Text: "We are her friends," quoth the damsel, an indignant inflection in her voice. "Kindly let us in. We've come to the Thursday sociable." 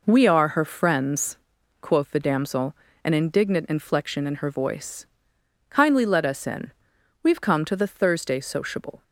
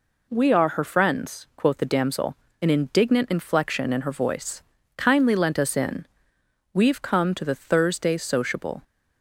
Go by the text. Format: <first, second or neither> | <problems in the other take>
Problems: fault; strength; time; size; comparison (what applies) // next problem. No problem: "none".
first | says "lent" for "let"; at 5.3 s